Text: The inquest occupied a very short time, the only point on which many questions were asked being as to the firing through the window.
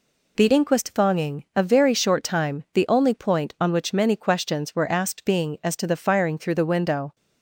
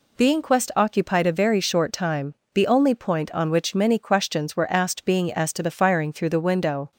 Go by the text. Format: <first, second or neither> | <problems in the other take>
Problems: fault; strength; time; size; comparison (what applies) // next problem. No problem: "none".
second | says "thonging" for "occupied"; at 0.9 s